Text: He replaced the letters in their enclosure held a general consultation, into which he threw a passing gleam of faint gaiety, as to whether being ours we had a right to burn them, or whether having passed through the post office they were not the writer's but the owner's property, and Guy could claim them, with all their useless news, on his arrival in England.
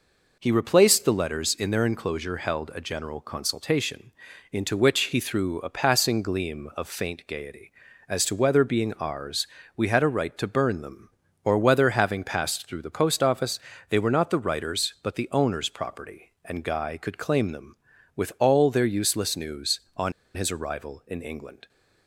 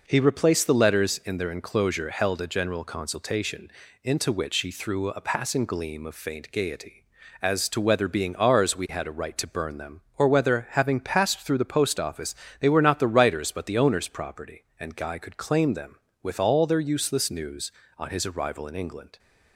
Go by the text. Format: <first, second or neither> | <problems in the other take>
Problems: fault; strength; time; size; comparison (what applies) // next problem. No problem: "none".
second | pauses between "ours" and "we"; slight; at 9.4 s; 0.28 s long // pauses between "office" and "they"; slight; at 13.5 s; 0.32 s long; slight in the second // pauses between "on" and "his"; slight; at 20.1 s; 0.24 s long